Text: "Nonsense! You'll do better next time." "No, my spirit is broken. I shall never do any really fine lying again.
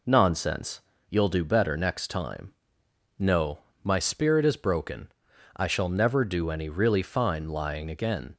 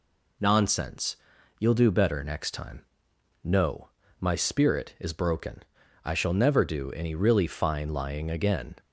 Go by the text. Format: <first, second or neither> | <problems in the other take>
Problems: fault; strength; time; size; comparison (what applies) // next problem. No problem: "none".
neither | none